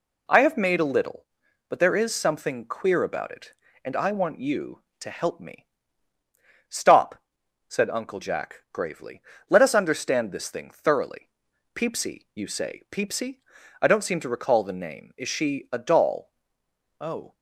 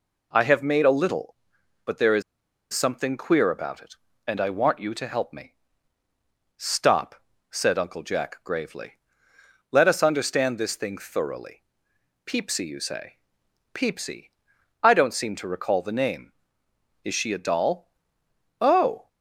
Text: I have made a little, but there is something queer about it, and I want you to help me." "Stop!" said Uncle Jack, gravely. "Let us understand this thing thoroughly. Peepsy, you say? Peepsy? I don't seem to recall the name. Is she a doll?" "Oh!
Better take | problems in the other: first | pauses between "is" and "something"; noticeable; at 2.2 s; 0.51 s long

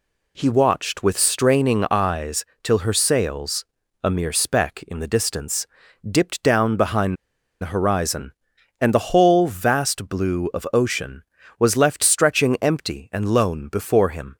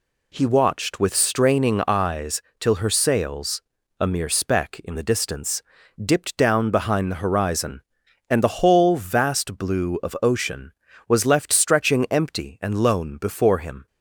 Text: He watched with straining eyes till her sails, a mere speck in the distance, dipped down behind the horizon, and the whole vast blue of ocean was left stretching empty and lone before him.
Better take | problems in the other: second | pauses between "eyes" and "till"; slight; at 2.4 s; 0.18 s long; slight in the second // pauses between "behind" and "the"; at 7.1 s; 0.45 s long

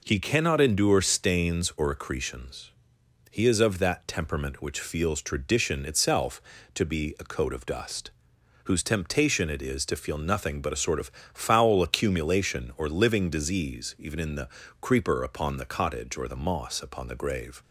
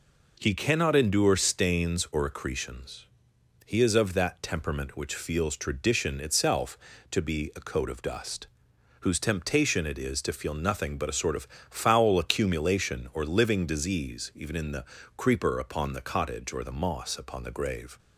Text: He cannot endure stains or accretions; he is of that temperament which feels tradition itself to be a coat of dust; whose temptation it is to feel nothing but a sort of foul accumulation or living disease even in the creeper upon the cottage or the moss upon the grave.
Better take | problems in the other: neither | pauses between "of" and "foul"; slight; the same in both // pauses between "the" and "creeper"; slight; the same in both

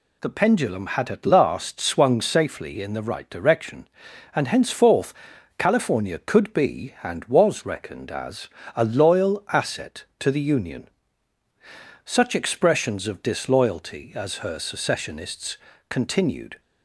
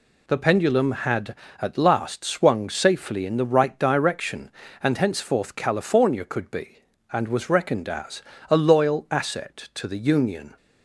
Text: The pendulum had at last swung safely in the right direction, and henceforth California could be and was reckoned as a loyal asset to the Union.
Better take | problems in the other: second | pauses between "henceforth" and "California"; at 5.1 s; 0.44 s long // pauses between "as" and "a"; slight; at 8.4 s; 0.28 s long; slight in the second // goes on to say "Such expressions of disloyalty as her secessionists continued"; strong; from 12.0 s on; 4.5 s long

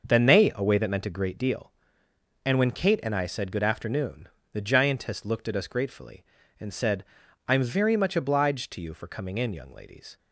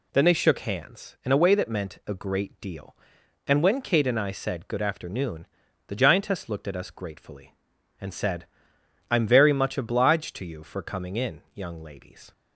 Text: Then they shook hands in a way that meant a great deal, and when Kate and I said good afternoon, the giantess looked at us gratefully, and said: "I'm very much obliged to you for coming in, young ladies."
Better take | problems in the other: second | starts louder than the rest; noticeable; until 1.1 s; 6 dB // skips "shook hands in"; at 0.5 s

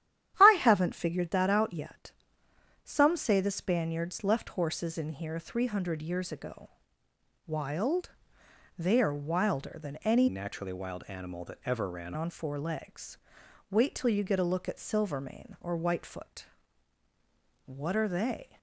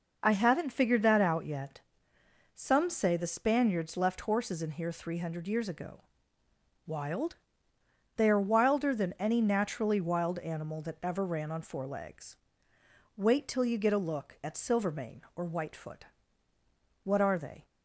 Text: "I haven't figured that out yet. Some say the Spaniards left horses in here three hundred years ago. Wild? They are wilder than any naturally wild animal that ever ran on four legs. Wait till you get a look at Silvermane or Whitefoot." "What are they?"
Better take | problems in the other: second | starts louder than the rest; strong; until 1.4 s; 11 dB // changes voice from "naturally" to "ran"; from 10.2 to 12.1 s; 1.9 s long

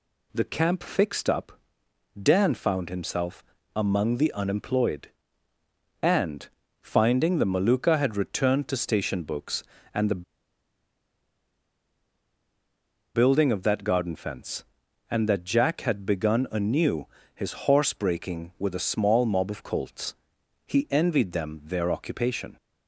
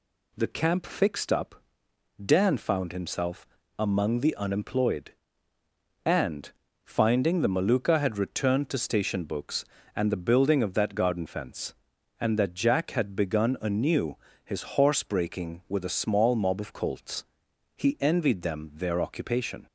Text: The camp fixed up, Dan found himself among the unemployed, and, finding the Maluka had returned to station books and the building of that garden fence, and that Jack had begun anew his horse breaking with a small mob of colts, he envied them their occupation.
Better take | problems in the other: second | pauses between "himself" and "among"; slight; at 3.4 s; 0.32 s long; slight in the second // pauses between "the" and "building"; strong; at 10.2 s; 2.9 s long // pauses between "anew" and "his"; slight; at 17.0 s; 0.28 s long; slight in the second // pauses between "his" and "horse"; slight; at 17.5 s; 0.16 s long; slight in the second

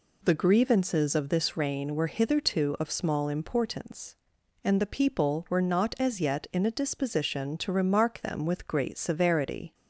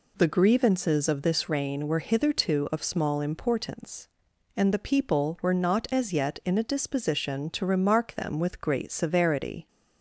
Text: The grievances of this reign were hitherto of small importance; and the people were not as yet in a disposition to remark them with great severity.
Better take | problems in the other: neither | none

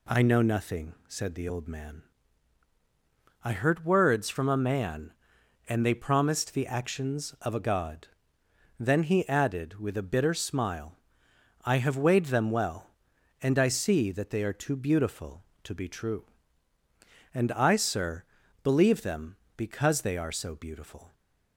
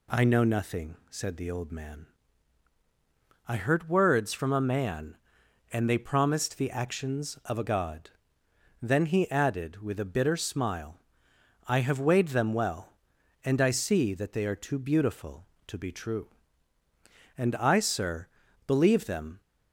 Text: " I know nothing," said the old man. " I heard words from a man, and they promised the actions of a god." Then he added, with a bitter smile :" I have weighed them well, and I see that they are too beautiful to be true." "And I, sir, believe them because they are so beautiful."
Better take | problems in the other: first | stops before "because they are so beautiful"; at 19.4 s

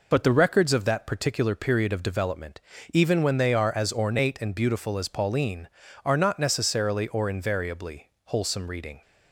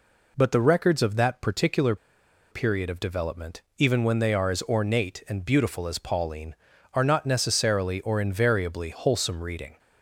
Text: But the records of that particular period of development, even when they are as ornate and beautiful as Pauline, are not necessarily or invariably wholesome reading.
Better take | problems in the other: first | pauses between "particular" and "period"; noticeable; at 1.9 s; 0.56 s long

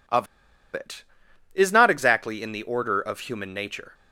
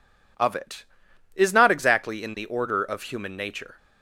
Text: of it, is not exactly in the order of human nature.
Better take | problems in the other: second | pauses between "of" and "it"; noticeable; at 0.2 s; 0.47 s long

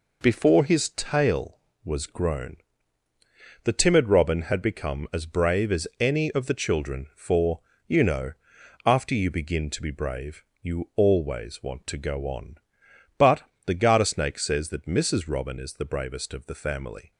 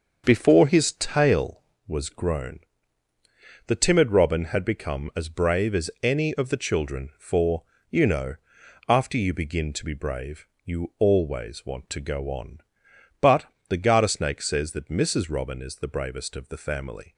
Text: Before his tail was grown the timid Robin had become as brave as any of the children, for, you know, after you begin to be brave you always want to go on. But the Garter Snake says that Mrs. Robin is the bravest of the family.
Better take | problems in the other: first | starts louder than the rest; until 1.8 s; 6.5 dB // pauses between "grown" and "the"; at 2.6 s; 1.0 s long; also in the first // pauses between "brave" and "you"; slight; at 10.4 s; 0.18 s long; slight in the first // pauses between "But" and "the"; slight; at 13.4 s; 0.24 s long; slight in the first

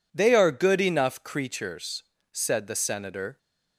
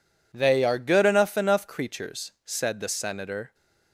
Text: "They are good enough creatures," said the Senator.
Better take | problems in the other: first | says "enough" twice; at 1.3 s

